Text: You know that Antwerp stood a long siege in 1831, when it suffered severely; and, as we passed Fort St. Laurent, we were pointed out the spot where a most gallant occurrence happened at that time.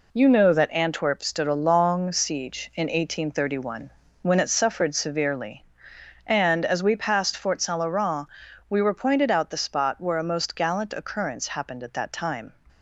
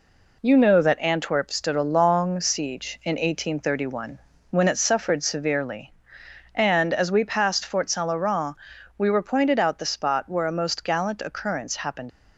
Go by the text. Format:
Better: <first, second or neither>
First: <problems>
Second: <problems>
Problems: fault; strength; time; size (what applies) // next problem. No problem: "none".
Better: first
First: none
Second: stops before "at that time"; at 12.0 s